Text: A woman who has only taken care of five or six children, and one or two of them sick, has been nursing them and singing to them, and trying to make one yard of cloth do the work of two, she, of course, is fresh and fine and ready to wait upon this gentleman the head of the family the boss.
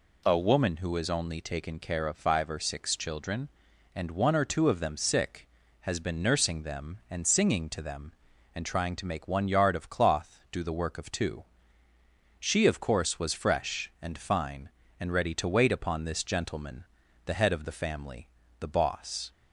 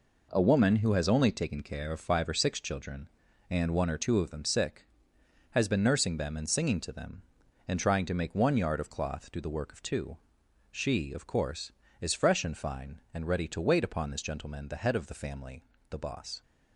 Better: second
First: says "was" for "is"; at 13.1 s // pauses between "gentleman" and "the"; at 16.8 s; 0.40 s long // pauses between "family" and "the"; slight; at 18.2 s; 0.32 s long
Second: pauses between "family" and "the"; slight; at 15.6 s; 0.28 s long

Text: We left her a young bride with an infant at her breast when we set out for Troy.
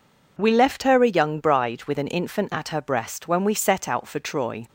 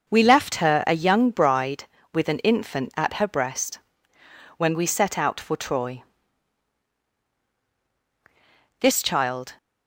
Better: first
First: none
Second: pauses between "breast" and "when"; noticeable; at 3.7 s; 0.78 s long // goes on to say "This child"; noticeable; from 8.7 s on; 0.78 s long

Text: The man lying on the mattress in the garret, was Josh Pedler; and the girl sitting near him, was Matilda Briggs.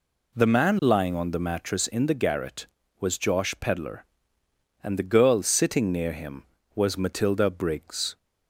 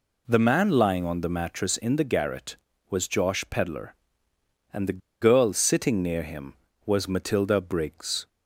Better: first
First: none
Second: pauses between "the" and "girl"; slight; at 4.9 s; 0.22 s long

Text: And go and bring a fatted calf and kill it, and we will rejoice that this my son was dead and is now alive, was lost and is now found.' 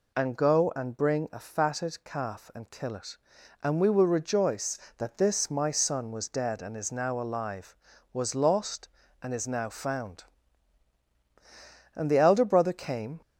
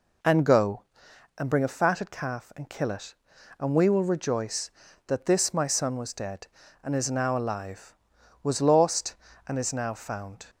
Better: second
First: goes on to say "And the elder brother came"; noticeable; from 11.9 s on; 1.2 s long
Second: none

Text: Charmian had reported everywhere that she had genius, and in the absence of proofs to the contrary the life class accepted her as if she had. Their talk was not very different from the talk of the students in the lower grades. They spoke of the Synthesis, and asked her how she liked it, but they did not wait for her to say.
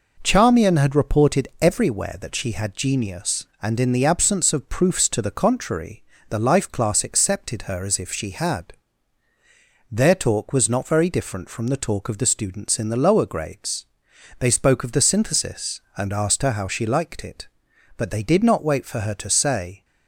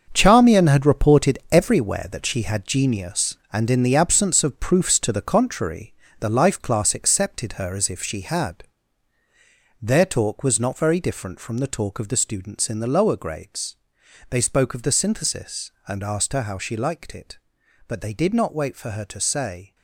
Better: first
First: pauses between "contrary" and "the"; slight; at 6.0 s; 0.26 s long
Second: gets quieter; strong; throughout; 10.5 dB // pauses between "contrary" and "the"; slight; at 5.9 s; 0.26 s long

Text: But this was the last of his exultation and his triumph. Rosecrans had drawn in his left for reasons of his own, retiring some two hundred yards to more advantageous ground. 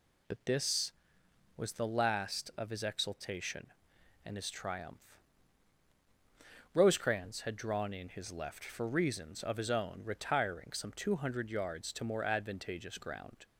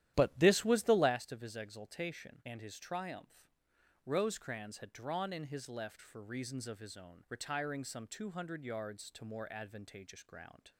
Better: first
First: none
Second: starts louder than the rest; strong; until 1.1 s; 12 dB

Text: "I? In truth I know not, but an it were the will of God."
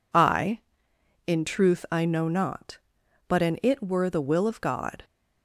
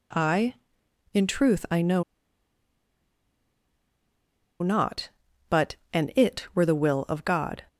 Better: first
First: none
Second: pauses between "know" and "not"; strong; at 2.0 s; 2.5 s long // pauses between "but" and "an"; slight; at 5.7 s; 0.18 s long

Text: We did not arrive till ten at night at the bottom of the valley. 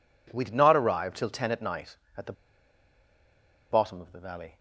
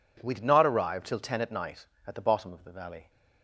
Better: second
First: pauses between "the" and "bottom"; strong; at 2.3 s; 1.3 s long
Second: none

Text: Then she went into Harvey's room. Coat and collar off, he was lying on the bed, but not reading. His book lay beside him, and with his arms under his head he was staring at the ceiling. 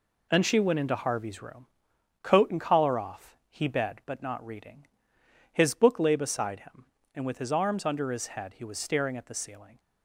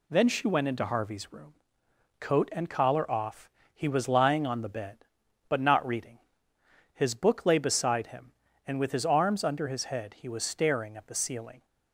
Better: second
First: skips "was lying on the"; at 3.6 s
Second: none

